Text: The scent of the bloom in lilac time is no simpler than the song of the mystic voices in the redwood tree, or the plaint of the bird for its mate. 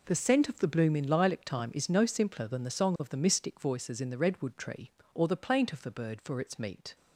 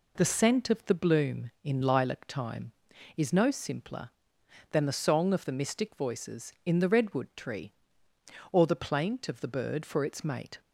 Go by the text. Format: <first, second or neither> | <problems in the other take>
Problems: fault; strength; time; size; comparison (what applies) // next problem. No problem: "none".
second | says "meat" for "mate"; at 6.5 s